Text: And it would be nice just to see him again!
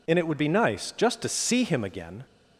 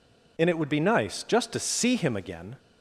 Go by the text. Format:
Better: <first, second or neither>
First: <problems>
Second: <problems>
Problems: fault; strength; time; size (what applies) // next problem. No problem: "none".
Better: neither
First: none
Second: none